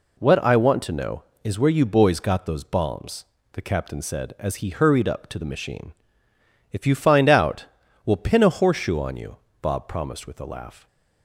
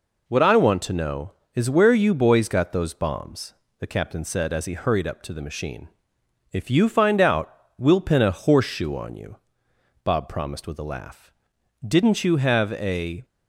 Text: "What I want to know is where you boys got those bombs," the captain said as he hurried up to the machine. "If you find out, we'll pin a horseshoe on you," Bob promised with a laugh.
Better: first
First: none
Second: goes on to say "Didn't you have a"; from 11.8 s on; 1.3 s long

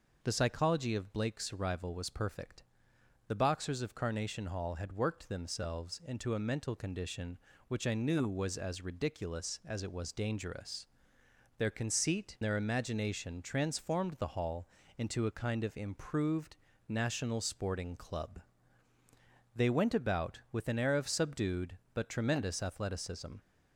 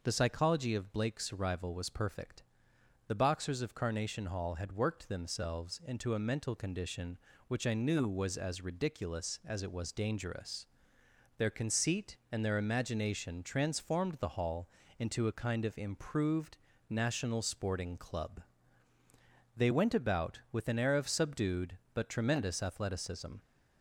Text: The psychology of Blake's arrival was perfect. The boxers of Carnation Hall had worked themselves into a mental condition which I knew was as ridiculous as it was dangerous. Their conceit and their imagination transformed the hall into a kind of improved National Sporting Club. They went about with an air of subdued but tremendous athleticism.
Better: second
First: skips "and"; at 12.3 s // pauses between "hall" and "into"; slight; at 14.6 s; 0.30 s long // pauses between "improved" and "National"; slight; at 16.5 s; 0.32 s long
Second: pauses between "hall" and "into"; slight; at 14.6 s; 0.30 s long // pauses between "improved" and "National"; slight; at 16.5 s; 0.32 s long

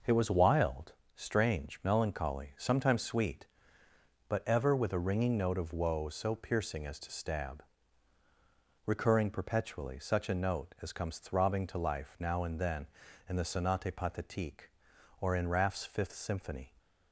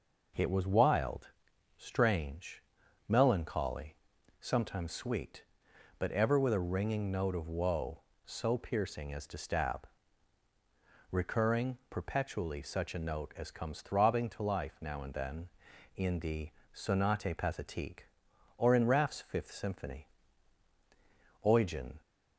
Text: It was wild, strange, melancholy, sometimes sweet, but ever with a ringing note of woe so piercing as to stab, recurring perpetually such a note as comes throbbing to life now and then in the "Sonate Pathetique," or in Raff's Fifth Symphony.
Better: first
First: none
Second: pauses between "the" and "Sonate"; slight; at 16.4 s; 0.24 s long // goes on to say "Eugen"; from 21.4 s on; 0.56 s long

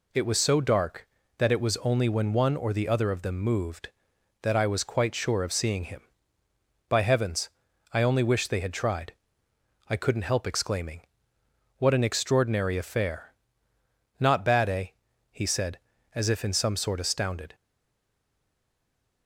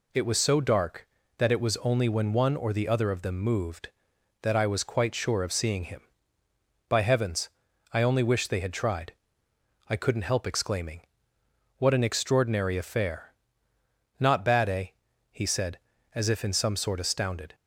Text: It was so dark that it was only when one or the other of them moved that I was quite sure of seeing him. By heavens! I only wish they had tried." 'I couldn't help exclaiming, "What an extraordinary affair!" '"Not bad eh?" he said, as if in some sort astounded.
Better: second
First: stays silent after the last word; noticeable; from 17.5 s on; 1.7 s long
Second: none

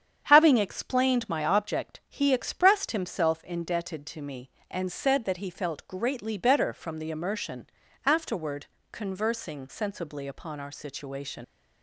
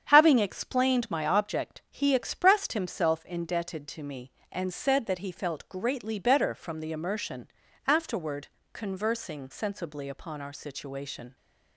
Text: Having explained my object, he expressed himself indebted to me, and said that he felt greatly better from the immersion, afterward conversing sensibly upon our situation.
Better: second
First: starts louder than the rest; strong; until 1.2 s; 8.5 dB // pauses between "afterward" and "conversing"; slight; at 8.6 s; 0.24 s long // leaves "situation" unfinished; at 11.4 s; 95 ms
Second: starts louder than the rest; strong; until 1.1 s; 8.5 dB // pauses between "afterward" and "conversing"; slight; at 8.4 s; 0.24 s long

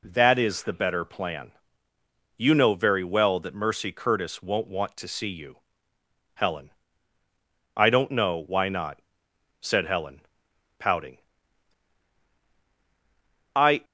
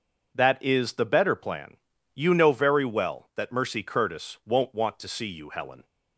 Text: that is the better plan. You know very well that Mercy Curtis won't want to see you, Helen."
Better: second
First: goes on to say "I don't know why not said Helen pouting I"; strong; from 7.7 s on; 6.1 s long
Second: none

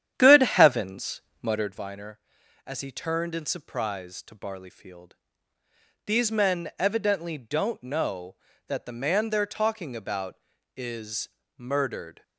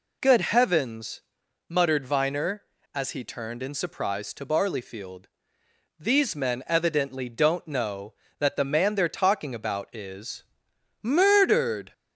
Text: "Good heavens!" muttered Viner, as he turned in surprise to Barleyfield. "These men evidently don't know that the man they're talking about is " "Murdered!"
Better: second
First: starts louder than the rest; strong; until 1.8 s; 10 dB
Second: none

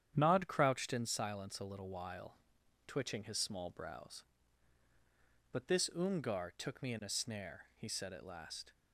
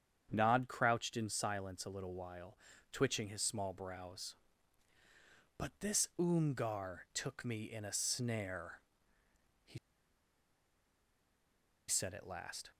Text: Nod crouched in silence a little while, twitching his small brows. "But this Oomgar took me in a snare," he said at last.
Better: first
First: starts louder than the rest; strong; until 1.1 s; 9.5 dB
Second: starts louder than the rest; strong; until 1.3 s; 8 dB // pauses between "he" and "said"; strong; at 9.7 s; 2.1 s long

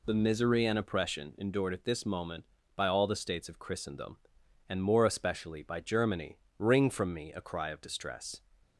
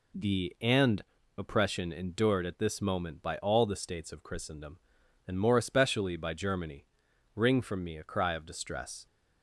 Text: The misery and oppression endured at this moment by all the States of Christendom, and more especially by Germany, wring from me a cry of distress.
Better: first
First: none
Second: skips "misery"; at 0.5 s // pauses between "and" and "oppression"; slight; at 1.0 s; 0.34 s long

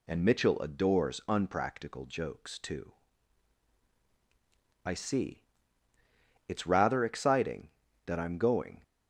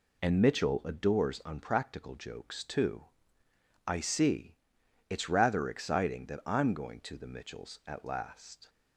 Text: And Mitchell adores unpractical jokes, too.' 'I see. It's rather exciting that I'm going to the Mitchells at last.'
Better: second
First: stops before "to the Mitchells at last"; at 8.8 s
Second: none

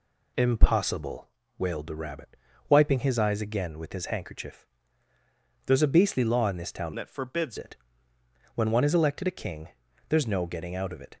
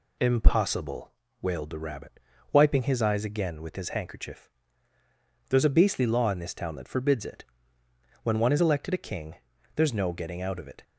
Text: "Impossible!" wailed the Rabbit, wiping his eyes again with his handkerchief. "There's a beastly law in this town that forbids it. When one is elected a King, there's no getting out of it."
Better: second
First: changes voice from "that" to "forbids"; from 6.9 to 7.5 s; 0.6 s long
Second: none

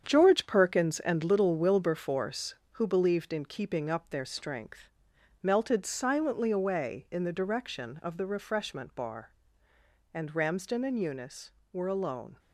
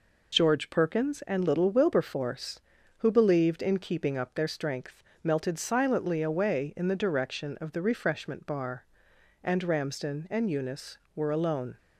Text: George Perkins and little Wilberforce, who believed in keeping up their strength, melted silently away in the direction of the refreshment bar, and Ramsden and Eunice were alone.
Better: second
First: gets quieter; strong; throughout; 8.5 dB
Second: none

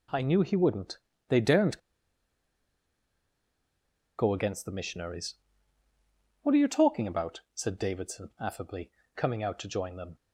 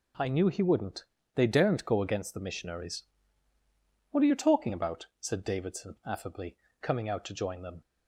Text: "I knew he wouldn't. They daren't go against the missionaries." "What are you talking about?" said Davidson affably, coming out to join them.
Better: second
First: pauses between "daren't" and "go"; strong; at 1.7 s; 2.4 s long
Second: none

